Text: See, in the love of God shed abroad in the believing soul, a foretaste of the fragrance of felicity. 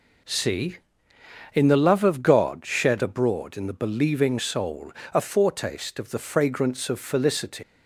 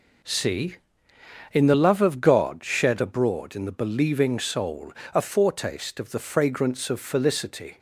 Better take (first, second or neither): second